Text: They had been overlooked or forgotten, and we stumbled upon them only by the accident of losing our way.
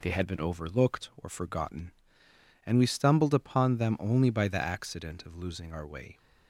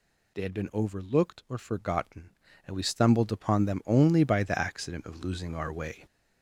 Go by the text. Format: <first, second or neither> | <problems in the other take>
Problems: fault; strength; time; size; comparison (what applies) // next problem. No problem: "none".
first | gets louder; noticeable; throughout; 6 dB